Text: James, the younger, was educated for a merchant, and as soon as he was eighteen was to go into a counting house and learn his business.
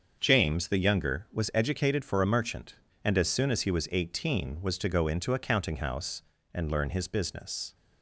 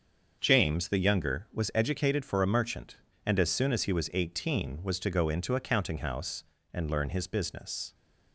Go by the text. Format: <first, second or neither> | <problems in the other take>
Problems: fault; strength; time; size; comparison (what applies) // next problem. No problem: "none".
neither | starts louder than the rest; the same in both